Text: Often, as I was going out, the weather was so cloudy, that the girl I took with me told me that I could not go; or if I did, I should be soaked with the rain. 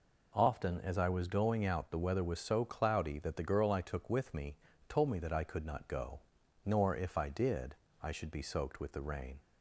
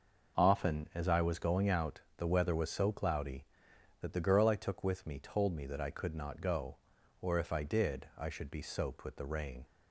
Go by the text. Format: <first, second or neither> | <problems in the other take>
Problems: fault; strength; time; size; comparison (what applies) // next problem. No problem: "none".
second | pauses between "me" and "told"; slight; at 4.5 s; 0.34 s long // says "nor" for "or"; at 6.6 s